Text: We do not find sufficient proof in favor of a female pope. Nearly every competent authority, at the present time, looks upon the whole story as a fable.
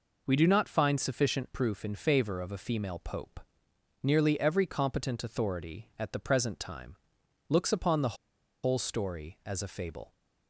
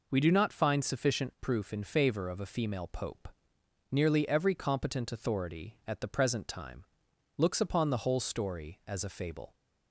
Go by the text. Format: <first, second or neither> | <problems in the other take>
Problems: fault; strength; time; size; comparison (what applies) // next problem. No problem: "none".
second | pauses between "the" and "whole"; noticeable; at 8.1 s; 0.48 s long